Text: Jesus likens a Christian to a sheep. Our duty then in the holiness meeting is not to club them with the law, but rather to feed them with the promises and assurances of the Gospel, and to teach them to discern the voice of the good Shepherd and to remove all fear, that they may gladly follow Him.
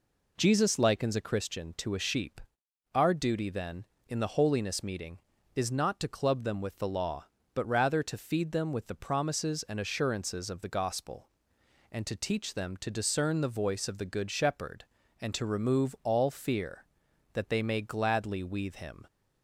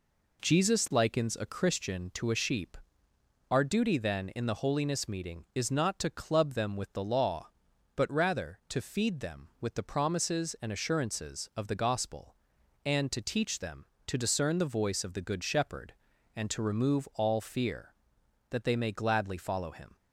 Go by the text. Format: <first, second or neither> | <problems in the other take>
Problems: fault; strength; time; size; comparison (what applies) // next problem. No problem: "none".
second | says "weathe" for "follow"; at 18.4 s